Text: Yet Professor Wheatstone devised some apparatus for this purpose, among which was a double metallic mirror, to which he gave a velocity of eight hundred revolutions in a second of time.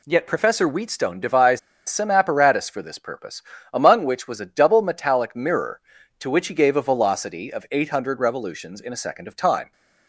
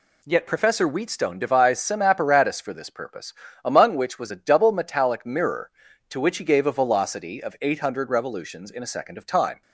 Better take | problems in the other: second | pauses between "devised" and "some"; slight; at 1.5 s; 0.29 s long

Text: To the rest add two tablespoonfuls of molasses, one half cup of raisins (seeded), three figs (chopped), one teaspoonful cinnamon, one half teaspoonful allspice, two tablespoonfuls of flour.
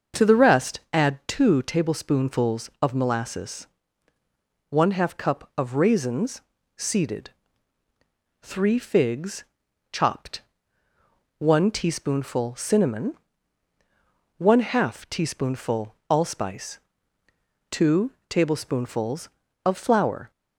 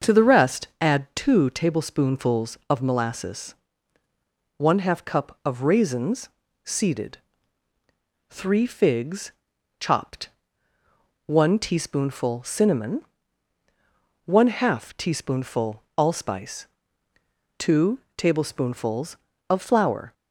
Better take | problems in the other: neither | starts louder than the rest; the same in both // pauses between "teaspoonful" and "allspice"; slight; the same in both // pauses between "two" and "tablespoonfuls"; slight; the same in both

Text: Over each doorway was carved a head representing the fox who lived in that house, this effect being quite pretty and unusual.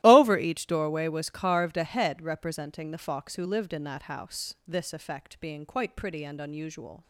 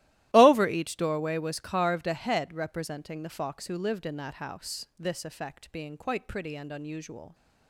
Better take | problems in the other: neither | starts louder than the rest; strong; the same in both

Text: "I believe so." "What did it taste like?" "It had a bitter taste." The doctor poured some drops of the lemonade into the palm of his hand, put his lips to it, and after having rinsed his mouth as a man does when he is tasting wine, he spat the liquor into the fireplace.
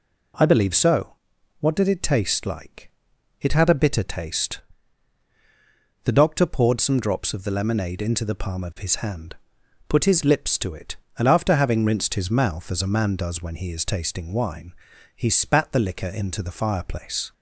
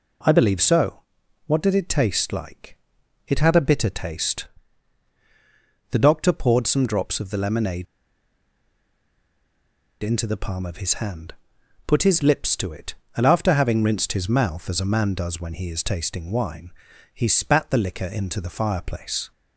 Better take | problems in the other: first | pauses between "lemonade" and "into"; strong; at 7.8 s; 2.1 s long

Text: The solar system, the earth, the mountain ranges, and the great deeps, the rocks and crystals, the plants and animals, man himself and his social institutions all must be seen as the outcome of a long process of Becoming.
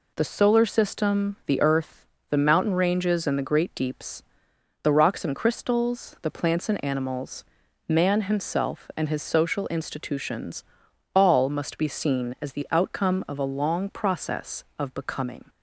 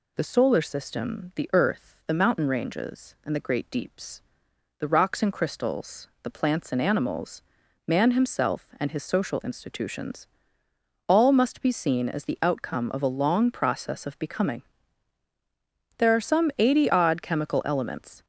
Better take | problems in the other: first | pauses between "institutions" and "all"; noticeable; at 10.2 s; 0.80 s long; noticeable in the first // goes on to say "There are some eighty odd chemical elements"; strong; from 15.9 s on; 2.2 s long

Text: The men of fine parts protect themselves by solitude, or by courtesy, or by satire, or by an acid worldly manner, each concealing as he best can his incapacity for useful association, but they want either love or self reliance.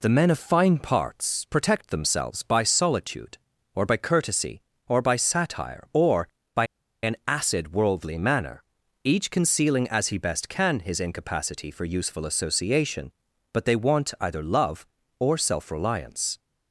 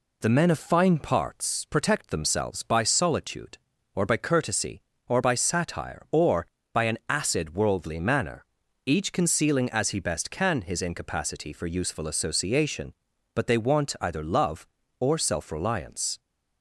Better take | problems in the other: second | pauses between "by" and "an"; at 6.6 s; 0.37 s long

